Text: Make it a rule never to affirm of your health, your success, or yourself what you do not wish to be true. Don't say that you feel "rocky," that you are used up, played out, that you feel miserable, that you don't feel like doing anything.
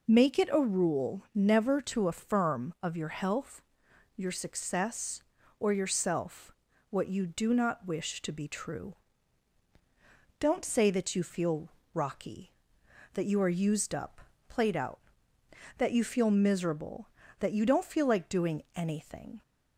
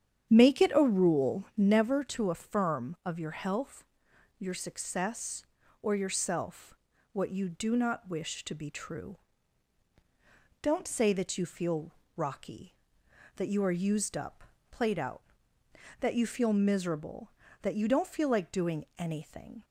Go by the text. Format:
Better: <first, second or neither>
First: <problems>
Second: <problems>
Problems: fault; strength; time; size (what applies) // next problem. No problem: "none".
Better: first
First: pauses between "yourself" and "what"; at 6.5 s; 0.38 s long // pauses between "feel" and "rocky"; slight; at 11.6 s; 0.22 s long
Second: starts louder than the rest; strong; until 1.8 s; 9 dB // pauses between "yourself" and "what"; at 6.7 s; 0.38 s long // pauses between "feel" and "rocky"; slight; at 11.9 s; 0.22 s long